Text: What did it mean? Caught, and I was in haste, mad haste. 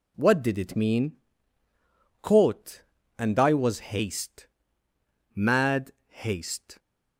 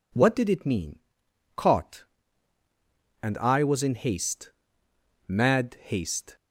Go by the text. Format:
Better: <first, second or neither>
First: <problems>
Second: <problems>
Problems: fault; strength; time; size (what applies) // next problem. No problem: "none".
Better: second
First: skips "in"; at 3.8 s // pauses between "mad" and "haste"; slight; at 5.9 s; 0.18 s long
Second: none